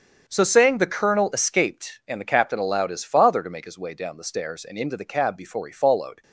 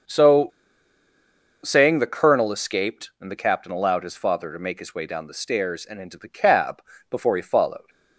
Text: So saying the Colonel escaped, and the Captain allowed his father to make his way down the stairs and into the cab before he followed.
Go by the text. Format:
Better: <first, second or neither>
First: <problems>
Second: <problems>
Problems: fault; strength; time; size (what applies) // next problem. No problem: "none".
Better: first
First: starts louder than the rest; strong; until 1.2 s; 7.5 dB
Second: starts louder than the rest; until 2.2 s; 6 dB // pauses between "So" and "saying"; at 0.4 s; 1.1 s long // pauses between "cab" and "before"; slight; at 6.8 s; 0.28 s long